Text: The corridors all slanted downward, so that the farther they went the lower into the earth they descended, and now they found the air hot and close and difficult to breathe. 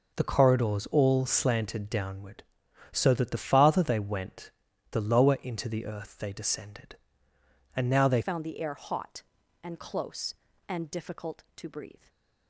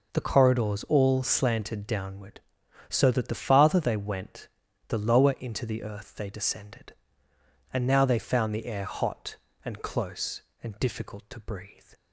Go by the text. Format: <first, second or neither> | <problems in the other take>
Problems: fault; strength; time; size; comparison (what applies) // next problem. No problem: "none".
second | pauses between "went" and "the"; at 4.5 s; 0.40 s long; also in the second // changes voice at "found"; from 8.2 s on; 3.8 s long // stays silent after the last word; slight; from 11.9 s on; 0.5 s long